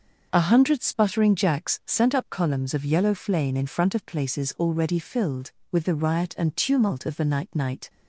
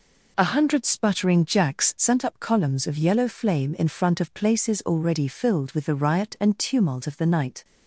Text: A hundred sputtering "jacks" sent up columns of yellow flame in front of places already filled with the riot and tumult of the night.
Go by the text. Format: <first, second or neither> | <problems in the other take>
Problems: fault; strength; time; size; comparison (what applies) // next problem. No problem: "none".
second | starts louder than the rest; noticeable; until 1.3 s; 6 dB // says "night" twice; at 7.5 s